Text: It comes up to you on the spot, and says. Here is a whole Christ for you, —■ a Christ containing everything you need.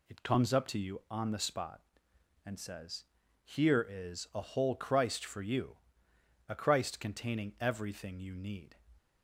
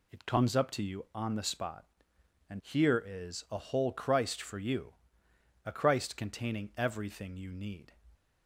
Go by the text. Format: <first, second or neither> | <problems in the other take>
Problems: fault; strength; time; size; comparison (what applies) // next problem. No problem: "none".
first | skips "says"; at 2.6 s